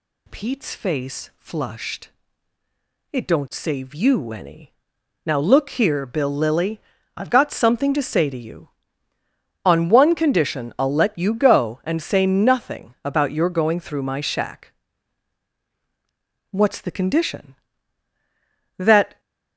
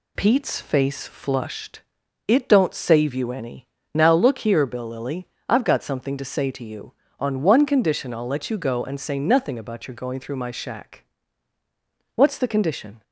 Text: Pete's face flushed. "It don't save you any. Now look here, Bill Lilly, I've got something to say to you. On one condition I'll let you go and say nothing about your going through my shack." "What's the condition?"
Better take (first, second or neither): second